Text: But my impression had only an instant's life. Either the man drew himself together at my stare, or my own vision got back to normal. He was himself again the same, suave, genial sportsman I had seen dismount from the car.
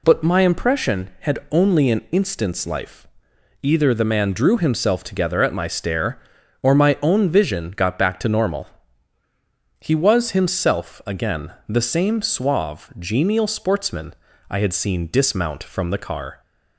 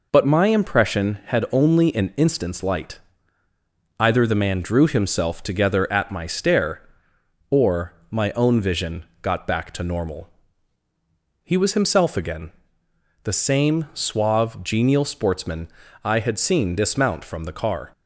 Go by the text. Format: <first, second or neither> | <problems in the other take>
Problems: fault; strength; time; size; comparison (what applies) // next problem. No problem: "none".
first | says "light" for "life"; at 2.6 s // pauses between "or" and "my"; slight; at 7.9 s; 0.16 s long // pauses between "vision" and "got"; slight; at 9.0 s; 0.18 s long // pauses between "again" and "the"; noticeable; at 12.5 s; 0.72 s long // pauses between "sportsman" and "I"; slight; at 15.6 s; 0.34 s long; also in the first